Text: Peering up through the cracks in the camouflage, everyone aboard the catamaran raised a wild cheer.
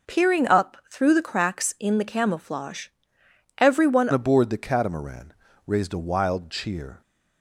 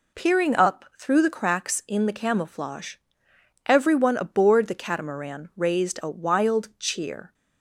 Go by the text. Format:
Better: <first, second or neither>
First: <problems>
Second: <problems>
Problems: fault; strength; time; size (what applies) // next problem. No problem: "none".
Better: second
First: changes voice at "aboard"; from 4.1 s on; 2.9 s long // pauses between "catamaran" and "raised"; slight; at 5.3 s; 0.32 s long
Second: none